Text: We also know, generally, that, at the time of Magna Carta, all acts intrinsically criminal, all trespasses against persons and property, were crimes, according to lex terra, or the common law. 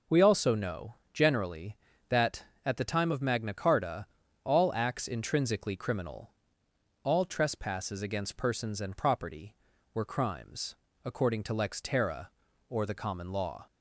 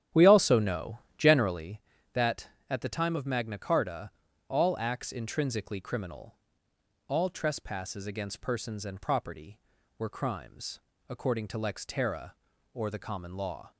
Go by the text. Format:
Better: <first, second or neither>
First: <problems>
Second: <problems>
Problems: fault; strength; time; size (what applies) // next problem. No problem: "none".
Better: first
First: none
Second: starts louder than the rest; strong; until 1.8 s; 10.5 dB